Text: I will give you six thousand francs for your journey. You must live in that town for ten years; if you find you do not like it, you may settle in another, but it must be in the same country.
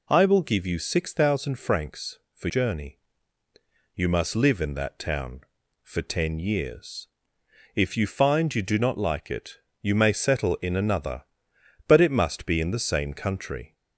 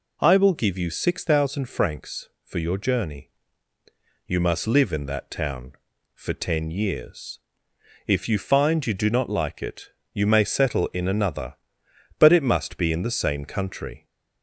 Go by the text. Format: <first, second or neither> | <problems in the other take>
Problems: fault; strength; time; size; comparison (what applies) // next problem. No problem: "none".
second | skips "your"; at 2.4 s